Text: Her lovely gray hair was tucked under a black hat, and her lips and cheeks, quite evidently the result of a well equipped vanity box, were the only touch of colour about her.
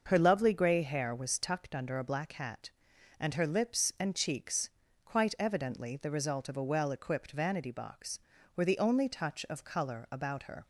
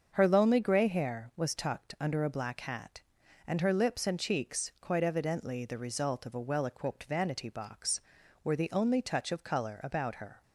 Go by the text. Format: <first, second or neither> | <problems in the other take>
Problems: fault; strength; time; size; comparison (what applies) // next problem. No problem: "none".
first | starts louder than the rest; until 1.1 s; 6.5 dB; noticeable in the first // says "lonely" for "lovely"; at 0.2 s